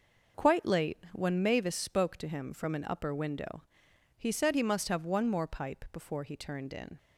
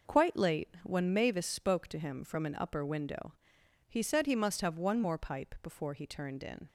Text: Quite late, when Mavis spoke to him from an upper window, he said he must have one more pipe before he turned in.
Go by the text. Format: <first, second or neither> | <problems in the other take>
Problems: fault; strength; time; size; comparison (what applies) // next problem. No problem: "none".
neither | none